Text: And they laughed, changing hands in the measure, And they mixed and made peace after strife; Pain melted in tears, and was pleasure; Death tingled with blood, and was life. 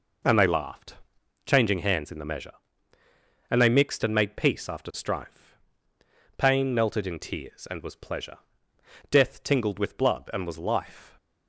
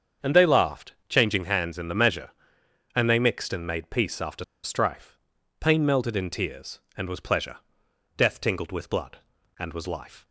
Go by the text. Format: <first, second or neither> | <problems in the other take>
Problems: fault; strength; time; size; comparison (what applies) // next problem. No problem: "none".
first | starts louder than the rest; strong; until 1.3 s; 7 dB // pauses between "after" and "strife"; slight; at 4.4 s; 0.20 s long